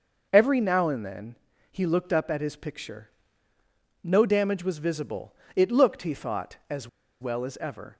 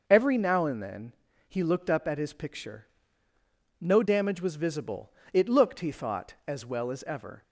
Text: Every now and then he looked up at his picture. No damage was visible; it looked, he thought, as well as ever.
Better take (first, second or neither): second